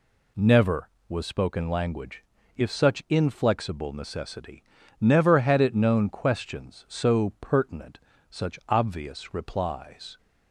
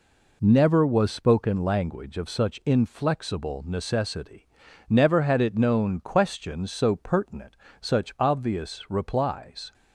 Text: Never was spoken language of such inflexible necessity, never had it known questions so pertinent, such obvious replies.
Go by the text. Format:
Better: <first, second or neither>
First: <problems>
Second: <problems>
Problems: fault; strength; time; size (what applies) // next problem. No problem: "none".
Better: second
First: says "if" for "of"; at 2.5 s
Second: none